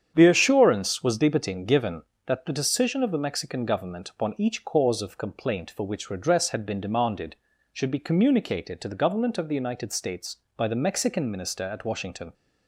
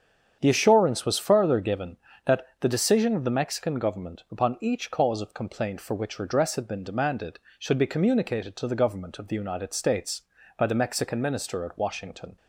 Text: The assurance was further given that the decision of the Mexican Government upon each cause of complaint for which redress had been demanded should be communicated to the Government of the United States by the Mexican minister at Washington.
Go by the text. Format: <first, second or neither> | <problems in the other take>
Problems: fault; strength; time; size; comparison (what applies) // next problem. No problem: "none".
second | starts louder than the rest; strong; until 1.1 s; 8.5 dB; strong in the second // says "debatin" for "further"; at 1.1 s